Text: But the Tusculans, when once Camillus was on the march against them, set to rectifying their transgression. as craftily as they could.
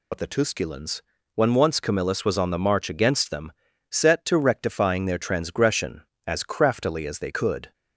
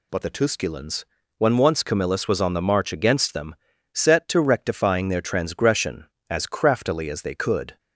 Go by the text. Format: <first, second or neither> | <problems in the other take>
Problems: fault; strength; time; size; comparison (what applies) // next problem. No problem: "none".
second | loses the start of "But"; at 0.1 s; 50 ms